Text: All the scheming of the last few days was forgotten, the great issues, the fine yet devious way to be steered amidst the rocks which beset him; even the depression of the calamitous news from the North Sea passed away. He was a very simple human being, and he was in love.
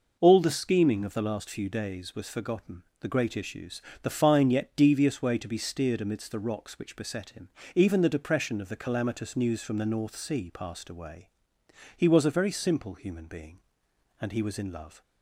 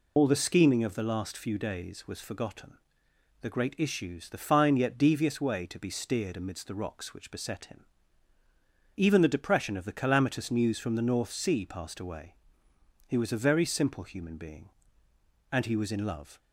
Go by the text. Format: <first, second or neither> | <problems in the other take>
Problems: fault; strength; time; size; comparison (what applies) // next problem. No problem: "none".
first | loses the start of "All"; at 0.1 s; 80 ms